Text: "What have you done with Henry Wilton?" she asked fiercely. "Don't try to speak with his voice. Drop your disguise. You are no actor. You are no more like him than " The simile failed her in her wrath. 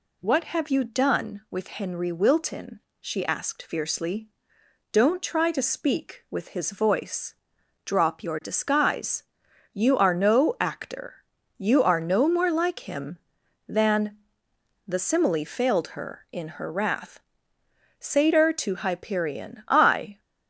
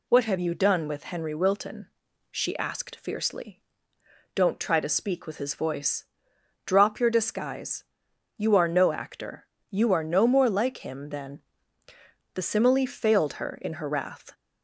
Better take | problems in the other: second | goes on to say "Satyr to Hyperion I"; strong; from 17.9 s on; 2.2 s long

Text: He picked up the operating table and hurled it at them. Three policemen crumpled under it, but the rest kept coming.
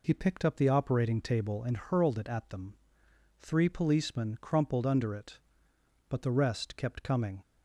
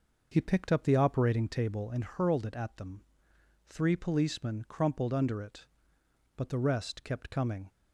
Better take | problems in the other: first | starts louder than the rest; noticeable; until 1.5 s; 6 dB

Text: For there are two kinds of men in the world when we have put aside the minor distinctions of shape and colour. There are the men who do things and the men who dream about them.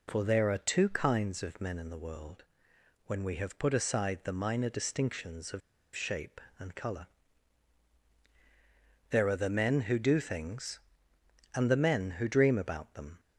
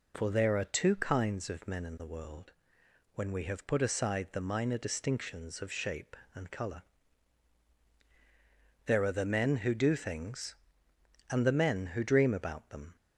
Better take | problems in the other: second | pauses between "world" and "when"; noticeable; at 2.4 s; 0.62 s long; noticeable in the second // pauses between "of" and "shape"; slight; at 5.6 s; 0.35 s long

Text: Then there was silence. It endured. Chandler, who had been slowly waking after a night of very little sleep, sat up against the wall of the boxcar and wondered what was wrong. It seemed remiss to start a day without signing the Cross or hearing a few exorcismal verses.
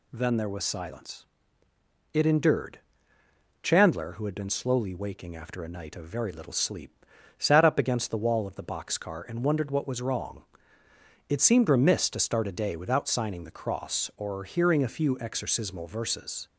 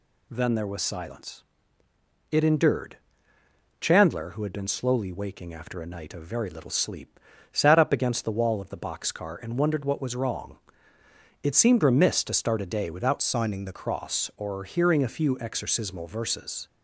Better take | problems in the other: first | changes voice from "signing" to "the"; from 13.2 to 13.7 s; 0.5 s long

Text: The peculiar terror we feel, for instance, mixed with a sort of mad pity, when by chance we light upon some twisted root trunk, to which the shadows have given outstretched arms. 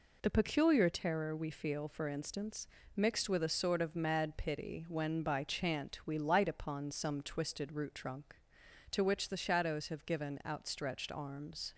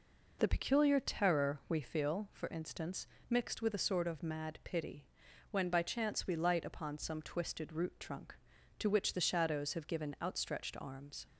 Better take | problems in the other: second | says "chant" for "chance"; at 5.4 s

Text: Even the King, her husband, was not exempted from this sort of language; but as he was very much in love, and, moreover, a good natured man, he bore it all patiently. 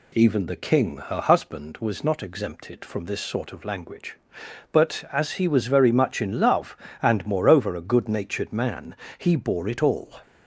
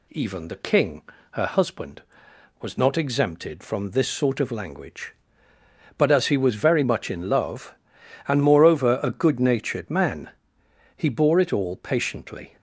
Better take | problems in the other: second | stops before "patiently"; at 10.2 s

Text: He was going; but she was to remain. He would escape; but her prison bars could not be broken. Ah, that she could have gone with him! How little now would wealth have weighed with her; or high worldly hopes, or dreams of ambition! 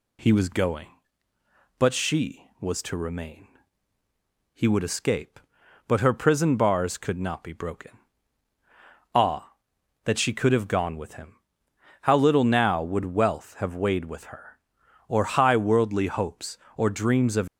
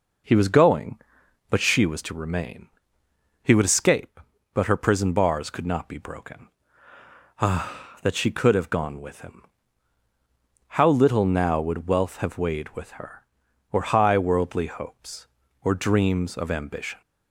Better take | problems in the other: second | stops before "ambition"; at 17.4 s

